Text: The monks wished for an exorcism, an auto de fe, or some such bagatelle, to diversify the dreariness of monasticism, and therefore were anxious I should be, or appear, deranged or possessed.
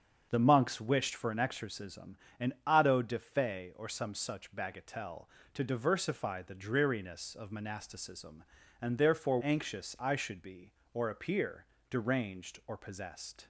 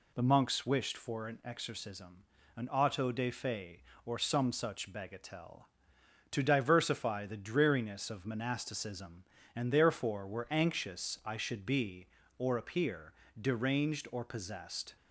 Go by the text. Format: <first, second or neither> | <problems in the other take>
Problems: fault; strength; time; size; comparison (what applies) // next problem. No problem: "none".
second | starts louder than the rest; until 1.3 s; 7 dB // skips "were"; at 9.4 s